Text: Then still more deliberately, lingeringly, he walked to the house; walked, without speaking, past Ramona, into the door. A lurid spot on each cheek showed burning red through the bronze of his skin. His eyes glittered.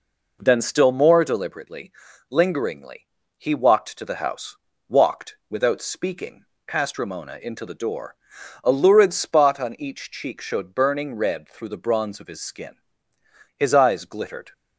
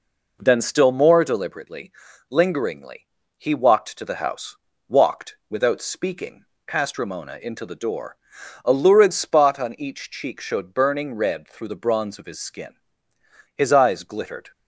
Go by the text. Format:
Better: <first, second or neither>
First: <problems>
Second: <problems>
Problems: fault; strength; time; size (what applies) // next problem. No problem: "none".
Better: neither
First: none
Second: none